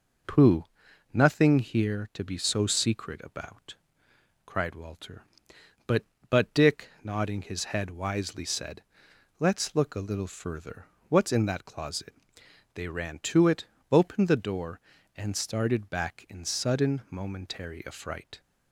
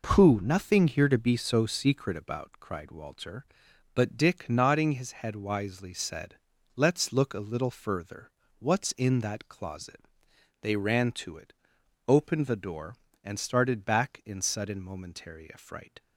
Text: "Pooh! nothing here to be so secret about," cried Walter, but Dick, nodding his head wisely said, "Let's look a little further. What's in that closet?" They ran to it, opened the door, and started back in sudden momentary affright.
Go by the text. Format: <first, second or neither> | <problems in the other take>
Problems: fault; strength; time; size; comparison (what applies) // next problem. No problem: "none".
second | says "but" twice; at 6.2 s